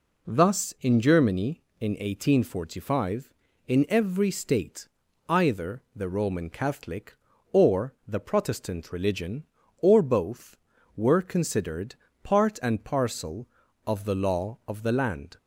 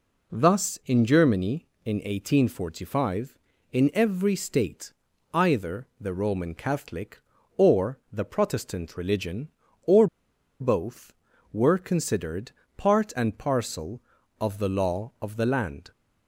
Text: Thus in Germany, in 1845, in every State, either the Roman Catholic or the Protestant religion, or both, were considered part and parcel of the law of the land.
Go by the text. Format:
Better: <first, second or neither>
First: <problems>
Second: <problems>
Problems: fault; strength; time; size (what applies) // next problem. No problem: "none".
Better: first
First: pauses between "considered" and "part"; slight; at 11.9 s; 0.28 s long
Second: pauses between "or" and "both"; noticeable; at 10.0 s; 0.54 s long // pauses between "considered" and "part"; slight; at 12.5 s; 0.26 s long